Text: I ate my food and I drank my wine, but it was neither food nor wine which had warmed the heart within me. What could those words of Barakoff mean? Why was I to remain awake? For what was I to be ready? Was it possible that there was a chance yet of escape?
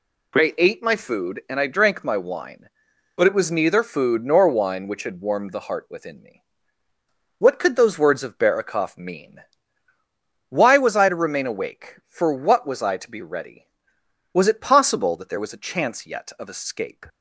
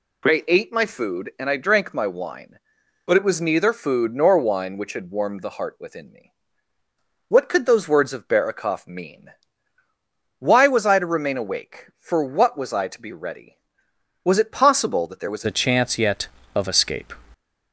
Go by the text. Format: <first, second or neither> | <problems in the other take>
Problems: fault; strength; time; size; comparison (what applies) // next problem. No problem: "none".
first | changes voice at "a"; from 15.4 s on; 1.7 s long